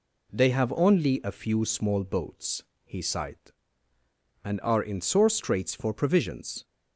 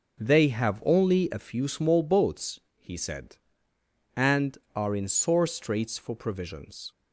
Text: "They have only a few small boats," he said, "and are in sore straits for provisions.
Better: second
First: says "sighed" for "said"; at 2.9 s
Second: none

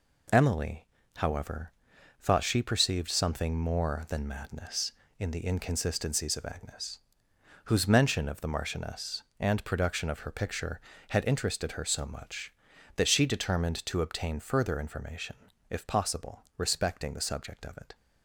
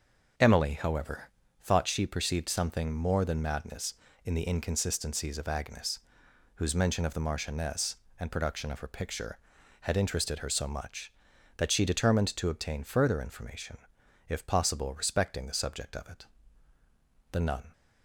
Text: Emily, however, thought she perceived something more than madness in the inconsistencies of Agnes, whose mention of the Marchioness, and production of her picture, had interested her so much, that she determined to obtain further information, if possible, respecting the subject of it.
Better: first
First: none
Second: starts louder than the rest; noticeable; until 1.7 s; 6 dB // goes on to say "The nun"; slight; from 17.3 s on; 0.40 s long

